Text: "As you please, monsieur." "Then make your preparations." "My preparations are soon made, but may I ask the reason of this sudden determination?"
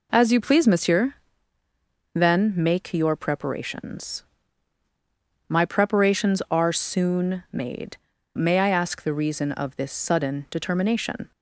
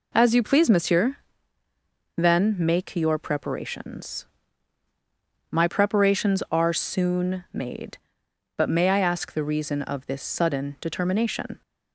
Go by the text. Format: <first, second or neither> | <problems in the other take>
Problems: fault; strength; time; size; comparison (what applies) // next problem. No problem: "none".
second | skips "but"; at 8.1 s